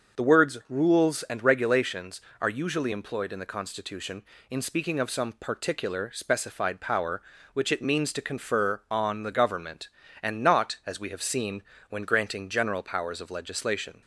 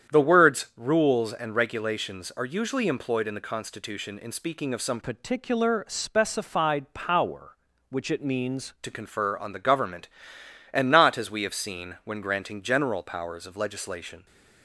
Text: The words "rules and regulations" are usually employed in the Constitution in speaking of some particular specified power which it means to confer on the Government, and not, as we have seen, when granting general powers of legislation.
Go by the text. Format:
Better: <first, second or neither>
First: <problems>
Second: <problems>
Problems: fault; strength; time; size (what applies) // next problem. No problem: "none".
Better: first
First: starts louder than the rest; until 1.2 s; 6.5 dB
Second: starts louder than the rest; strong; until 1.2 s; 9 dB // changes voice from "particular" to "means"; from 5.0 to 8.7 s; 3.7 s long